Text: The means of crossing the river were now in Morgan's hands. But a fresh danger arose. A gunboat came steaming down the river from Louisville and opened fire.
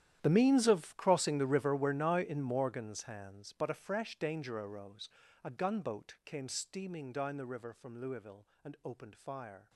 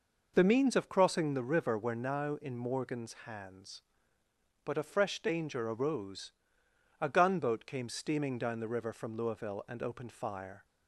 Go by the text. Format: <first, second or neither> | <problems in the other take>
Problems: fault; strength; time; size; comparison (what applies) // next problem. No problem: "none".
second | gets quieter; strong; throughout; 18 dB